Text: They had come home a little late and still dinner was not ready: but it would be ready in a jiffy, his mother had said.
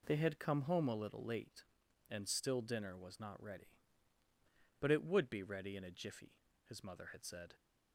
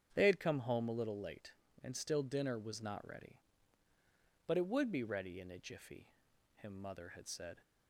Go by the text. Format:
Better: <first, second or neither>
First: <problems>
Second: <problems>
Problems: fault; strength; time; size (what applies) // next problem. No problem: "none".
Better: first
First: none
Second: starts louder than the rest; strong; until 1.1 s; 8 dB // says "him" for "his"; at 6.5 s